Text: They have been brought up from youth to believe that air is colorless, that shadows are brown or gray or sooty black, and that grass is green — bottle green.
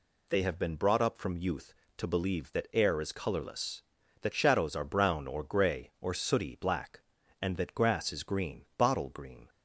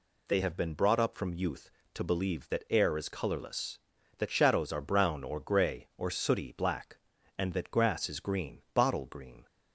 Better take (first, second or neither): neither